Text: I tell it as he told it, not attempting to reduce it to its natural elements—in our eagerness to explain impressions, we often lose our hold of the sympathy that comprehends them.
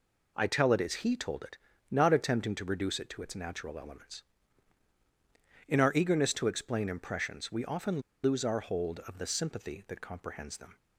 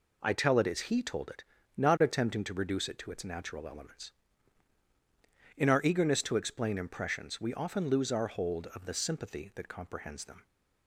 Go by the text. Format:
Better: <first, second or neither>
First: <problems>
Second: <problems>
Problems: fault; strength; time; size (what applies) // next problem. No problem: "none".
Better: second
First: pauses between "often" and "lose"; slight; at 7.9 s; 0.23 s long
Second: none